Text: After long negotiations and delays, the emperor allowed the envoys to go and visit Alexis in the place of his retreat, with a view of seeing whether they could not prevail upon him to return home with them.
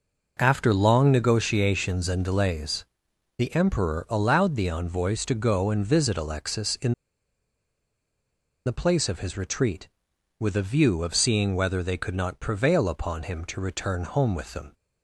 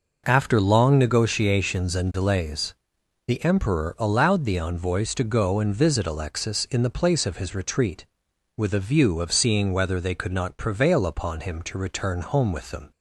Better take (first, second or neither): second